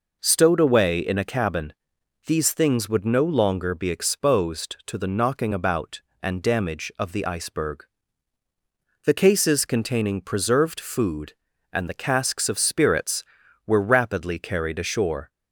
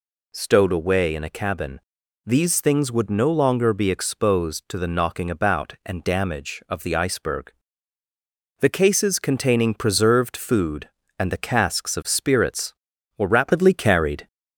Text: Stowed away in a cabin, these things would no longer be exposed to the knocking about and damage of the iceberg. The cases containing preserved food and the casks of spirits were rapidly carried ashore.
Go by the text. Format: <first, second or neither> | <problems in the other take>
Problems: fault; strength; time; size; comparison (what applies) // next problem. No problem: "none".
first | stops before "ashore"; at 14.2 s